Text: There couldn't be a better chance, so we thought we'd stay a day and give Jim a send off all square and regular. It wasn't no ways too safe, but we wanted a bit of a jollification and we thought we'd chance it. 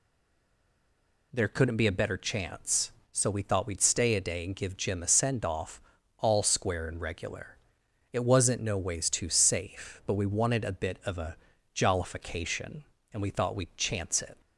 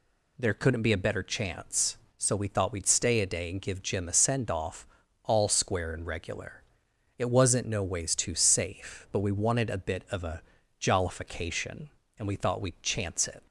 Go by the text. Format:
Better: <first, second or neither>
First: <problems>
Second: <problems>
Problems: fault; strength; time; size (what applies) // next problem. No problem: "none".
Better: second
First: stays silent before the first word; noticeable; until 1.3 s; 1.3 s long // pauses between "off" and "all"; at 5.8 s; 0.38 s long // pauses between "a" and "jollification"; slight; at 11.3 s; 0.36 s long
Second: pauses between "off" and "all"; at 4.8 s; 0.38 s long // pauses between "a" and "jollification"; slight; at 10.4 s; 0.36 s long